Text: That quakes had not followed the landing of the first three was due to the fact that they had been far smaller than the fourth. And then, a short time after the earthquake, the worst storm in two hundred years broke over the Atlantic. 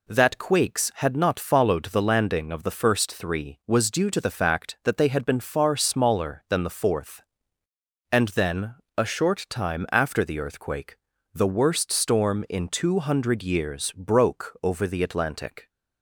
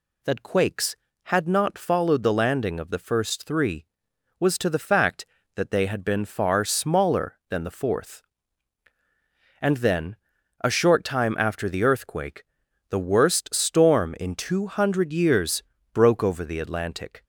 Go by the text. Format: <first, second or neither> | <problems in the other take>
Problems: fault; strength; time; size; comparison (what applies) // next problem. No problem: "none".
first | skips "due"; at 4.5 s // pauses between "years" and "broke"; slight; at 15.6 s; 0.30 s long